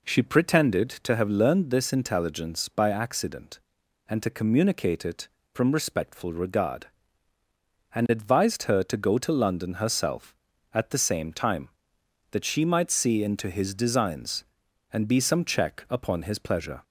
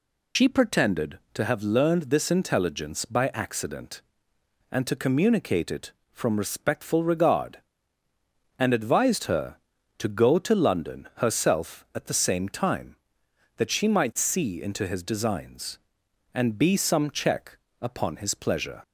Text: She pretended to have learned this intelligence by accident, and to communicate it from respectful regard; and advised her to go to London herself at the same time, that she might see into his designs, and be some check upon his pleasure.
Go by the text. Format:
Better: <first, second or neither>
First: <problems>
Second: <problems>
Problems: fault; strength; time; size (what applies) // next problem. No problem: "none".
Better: first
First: none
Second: loses the start of "She"; at 0.3 s; 95 ms // pauses between "check" and "upon"; slight; at 17.5 s; 0.24 s long